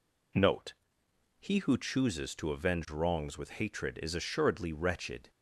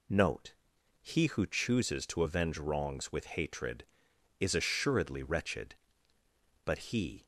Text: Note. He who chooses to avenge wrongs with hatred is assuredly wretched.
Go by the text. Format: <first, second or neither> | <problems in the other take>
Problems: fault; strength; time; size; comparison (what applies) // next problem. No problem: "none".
first | goes on to say "But he"; from 6.6 s on; 0.58 s long